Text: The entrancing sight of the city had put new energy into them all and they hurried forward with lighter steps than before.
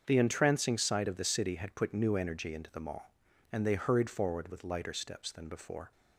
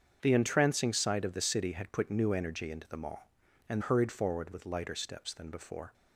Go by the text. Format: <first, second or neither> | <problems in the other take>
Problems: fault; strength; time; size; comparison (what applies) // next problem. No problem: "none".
first | starts louder than the rest; strong; until 1.2 s; 7 dB; also in the first // skips "they"; at 3.8 s